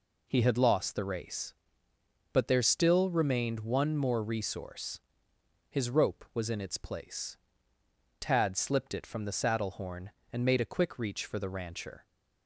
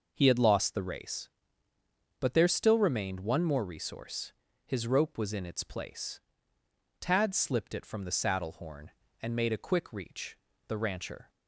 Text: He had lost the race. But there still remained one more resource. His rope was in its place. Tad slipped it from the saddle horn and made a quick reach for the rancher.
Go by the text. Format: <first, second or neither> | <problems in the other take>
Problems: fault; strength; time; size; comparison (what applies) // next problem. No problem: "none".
first | skips "for"; at 10.5 s